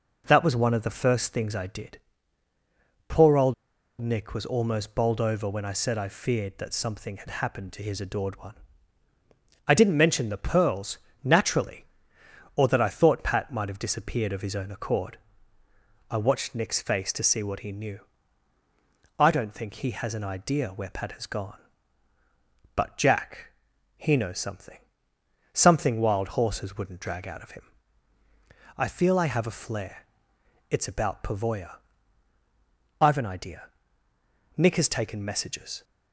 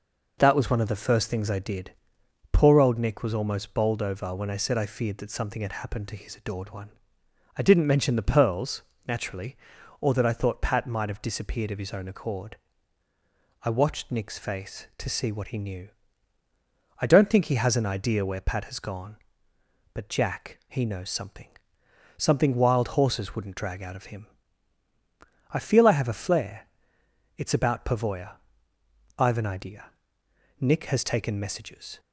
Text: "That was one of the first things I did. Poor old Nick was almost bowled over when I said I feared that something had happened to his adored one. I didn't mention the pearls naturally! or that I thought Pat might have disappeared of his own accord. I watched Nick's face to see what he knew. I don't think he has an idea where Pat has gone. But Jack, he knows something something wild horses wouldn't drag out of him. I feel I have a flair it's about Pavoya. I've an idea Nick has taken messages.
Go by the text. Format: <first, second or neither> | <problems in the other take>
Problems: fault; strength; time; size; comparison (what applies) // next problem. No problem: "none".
second | pauses between "old" and "Nick"; noticeable; at 3.5 s; 0.47 s long // pauses between "pearls" and "naturally"; slight; at 10.9 s; 0.26 s long; slight in the second // pauses between "something" and "something"; noticeable; at 24.7 s; 0.76 s long; noticeable in the second // pauses between "flair" and "it's"; noticeable; at 30.0 s; 0.64 s long; noticeable in the second // pauses between "idea" and "Nick"; noticeable; at 33.6 s; 0.94 s long; noticeable in the second